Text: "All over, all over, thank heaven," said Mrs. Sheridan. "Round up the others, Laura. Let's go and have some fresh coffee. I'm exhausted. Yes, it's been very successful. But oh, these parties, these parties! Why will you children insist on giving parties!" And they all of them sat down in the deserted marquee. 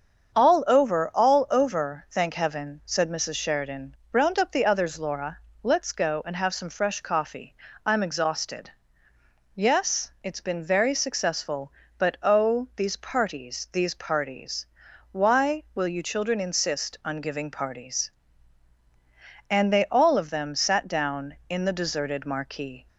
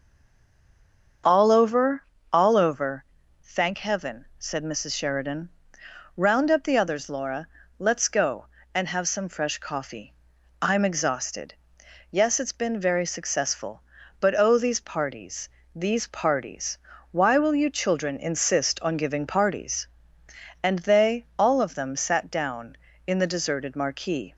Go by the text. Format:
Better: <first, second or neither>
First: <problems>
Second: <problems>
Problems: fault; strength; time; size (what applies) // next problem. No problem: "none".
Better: first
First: starts louder than the rest; until 1.3 s; 7 dB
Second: stays silent before the first word; noticeable; until 1.2 s; 1.2 s long // starts louder than the rest; until 2.5 s; 6.5 dB